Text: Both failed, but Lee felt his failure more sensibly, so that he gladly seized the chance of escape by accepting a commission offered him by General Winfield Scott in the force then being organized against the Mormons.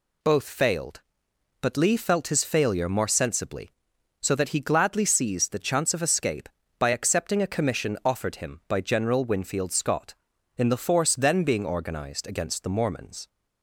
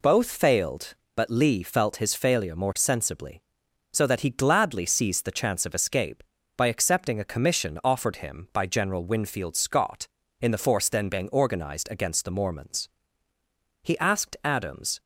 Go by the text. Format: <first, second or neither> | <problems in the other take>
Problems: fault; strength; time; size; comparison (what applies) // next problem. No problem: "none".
first | goes on to say "He asked Adams"; noticeable; from 13.8 s on; 1.1 s long